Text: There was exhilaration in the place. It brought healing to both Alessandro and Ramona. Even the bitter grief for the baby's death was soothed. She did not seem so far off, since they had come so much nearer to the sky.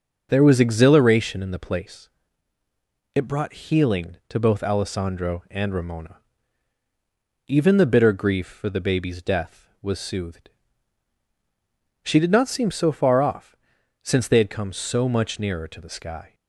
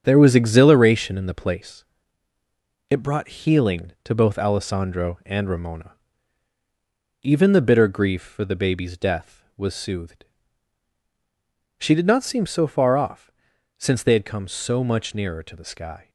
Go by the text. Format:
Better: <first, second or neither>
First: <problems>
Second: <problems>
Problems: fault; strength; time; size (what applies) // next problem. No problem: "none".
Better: first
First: starts louder than the rest; until 1.3 s; 6.5 dB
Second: gets quieter; strong; throughout; 7 dB // starts louder than the rest; strong; until 1.0 s; 7.5 dB